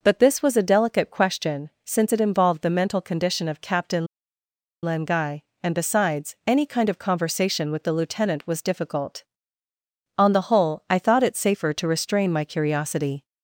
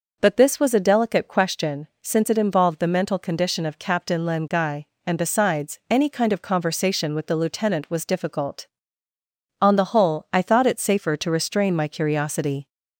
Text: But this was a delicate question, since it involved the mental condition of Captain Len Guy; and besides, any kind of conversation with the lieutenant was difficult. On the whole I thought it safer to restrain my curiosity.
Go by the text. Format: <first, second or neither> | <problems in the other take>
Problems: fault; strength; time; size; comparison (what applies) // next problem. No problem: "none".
second | pauses between "Captain" and "Len"; noticeable; at 4.0 s; 0.78 s long